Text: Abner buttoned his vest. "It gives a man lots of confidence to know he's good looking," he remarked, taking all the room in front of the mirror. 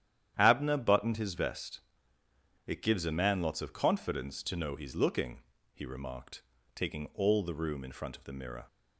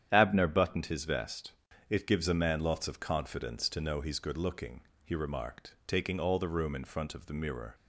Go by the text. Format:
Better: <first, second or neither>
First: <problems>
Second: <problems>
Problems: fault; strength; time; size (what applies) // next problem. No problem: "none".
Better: second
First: starts louder than the rest; strong; until 1.3 s; 10.5 dB // skips "good"; at 4.9 s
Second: starts louder than the rest; strong; until 1.1 s; 9.5 dB